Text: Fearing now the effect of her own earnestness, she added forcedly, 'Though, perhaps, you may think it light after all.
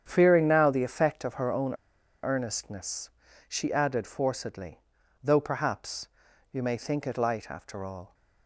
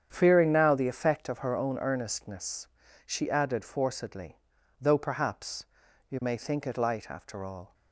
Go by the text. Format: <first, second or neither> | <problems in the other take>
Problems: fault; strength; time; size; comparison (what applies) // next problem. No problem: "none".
second | starts louder than the rest; strong; until 1.0 s; 8.5 dB; strong in the second // pauses between "own" and "earnestness"; noticeable; at 1.7 s; 0.48 s long